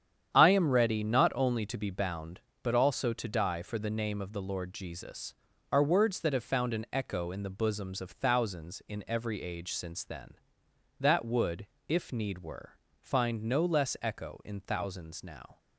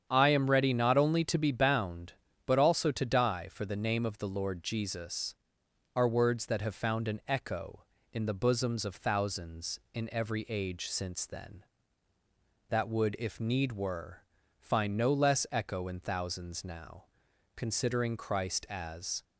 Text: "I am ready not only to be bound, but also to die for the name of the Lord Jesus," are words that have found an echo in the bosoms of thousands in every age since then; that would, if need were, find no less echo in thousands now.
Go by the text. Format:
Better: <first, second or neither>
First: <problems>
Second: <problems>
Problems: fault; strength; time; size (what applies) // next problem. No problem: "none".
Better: first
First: starts louder than the rest; strong; until 1.3 s; 9 dB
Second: starts louder than the rest; strong; until 1.1 s; 8 dB // goes on to say "Considering Christ as"; strong; from 17.5 s on; 1.6 s long